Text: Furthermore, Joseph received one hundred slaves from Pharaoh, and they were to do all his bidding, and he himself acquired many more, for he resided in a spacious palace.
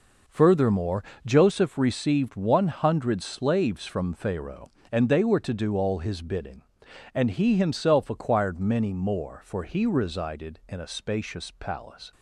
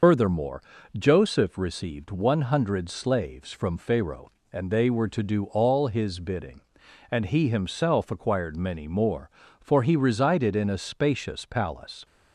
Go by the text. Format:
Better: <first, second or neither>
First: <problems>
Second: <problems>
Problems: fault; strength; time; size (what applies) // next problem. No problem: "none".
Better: first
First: none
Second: loses the start of "Furthermore"; at 0.0 s; 80 ms